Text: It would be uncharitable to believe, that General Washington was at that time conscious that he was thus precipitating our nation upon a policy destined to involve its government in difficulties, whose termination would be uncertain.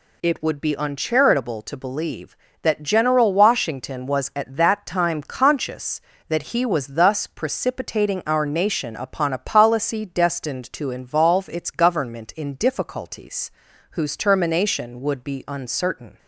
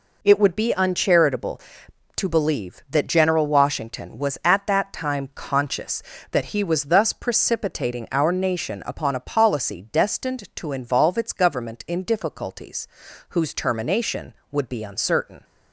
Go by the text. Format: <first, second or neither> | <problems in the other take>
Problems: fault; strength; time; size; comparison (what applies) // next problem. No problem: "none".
neither | none